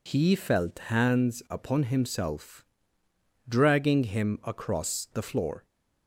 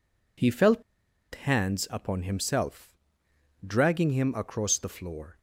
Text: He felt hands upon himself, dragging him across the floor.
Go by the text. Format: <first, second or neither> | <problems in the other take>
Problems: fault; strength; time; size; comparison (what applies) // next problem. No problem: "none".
first | pauses between "felt" and "hands"; noticeable; at 0.8 s; 0.51 s long